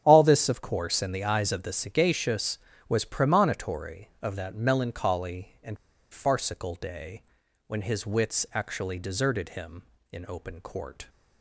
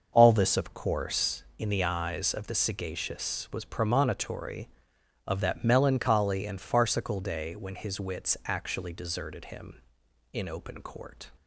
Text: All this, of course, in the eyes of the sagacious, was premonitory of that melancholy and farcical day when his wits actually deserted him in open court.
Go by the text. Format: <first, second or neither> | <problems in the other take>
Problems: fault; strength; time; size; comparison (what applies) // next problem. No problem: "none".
second | starts louder than the rest; strong; until 1.0 s; 9 dB; noticeable in the second // pauses between "and" and "farcical"; at 5.7 s; 0.36 s long // pauses between "day" and "when"; at 7.2 s; 0.44 s long